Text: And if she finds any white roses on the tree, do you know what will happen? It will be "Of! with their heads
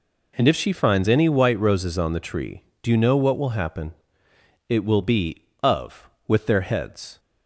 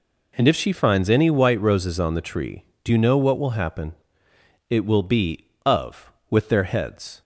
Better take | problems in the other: neither | none

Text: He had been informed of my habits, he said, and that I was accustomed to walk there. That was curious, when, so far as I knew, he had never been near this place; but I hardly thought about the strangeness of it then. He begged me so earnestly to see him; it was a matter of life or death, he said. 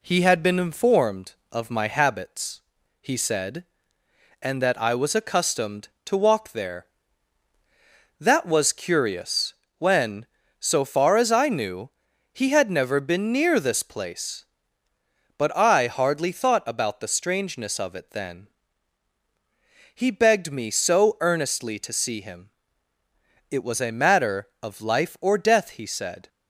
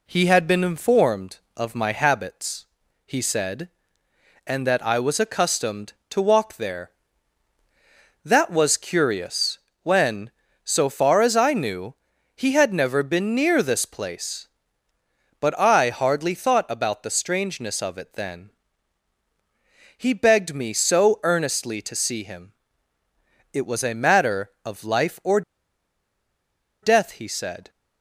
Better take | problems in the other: first | pauses between "or" and "death"; strong; at 25.4 s; 1.4 s long

